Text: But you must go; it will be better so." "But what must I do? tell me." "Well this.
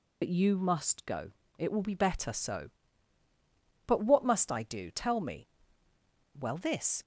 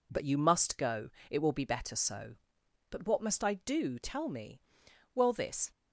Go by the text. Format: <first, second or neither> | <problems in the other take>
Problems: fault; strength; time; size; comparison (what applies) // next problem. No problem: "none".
second | loses the start of "But"; at 0.2 s; 60 ms